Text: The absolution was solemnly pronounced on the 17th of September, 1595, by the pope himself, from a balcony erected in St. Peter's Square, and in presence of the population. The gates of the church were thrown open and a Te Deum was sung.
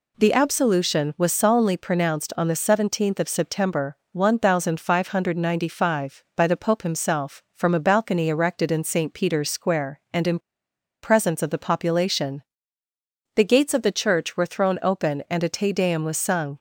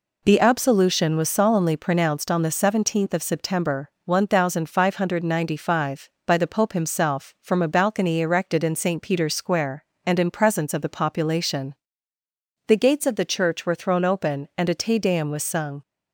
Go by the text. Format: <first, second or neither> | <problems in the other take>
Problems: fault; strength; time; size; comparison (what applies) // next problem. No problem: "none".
second | pauses between "in" and "presence"; noticeable; at 10.3 s; 0.64 s long